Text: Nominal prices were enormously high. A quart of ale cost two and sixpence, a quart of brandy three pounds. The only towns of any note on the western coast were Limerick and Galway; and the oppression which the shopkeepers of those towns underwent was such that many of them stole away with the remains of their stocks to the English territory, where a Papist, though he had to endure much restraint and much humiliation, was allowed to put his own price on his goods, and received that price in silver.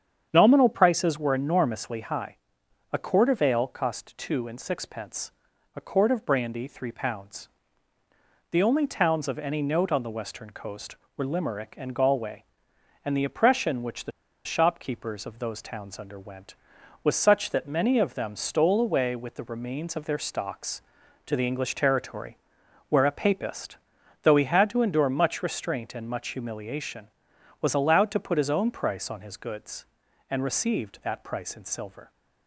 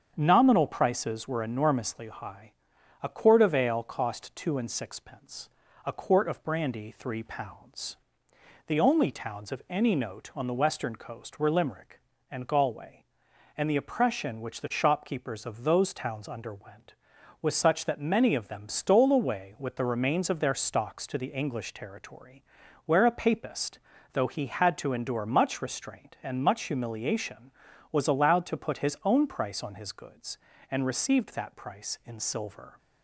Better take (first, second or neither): second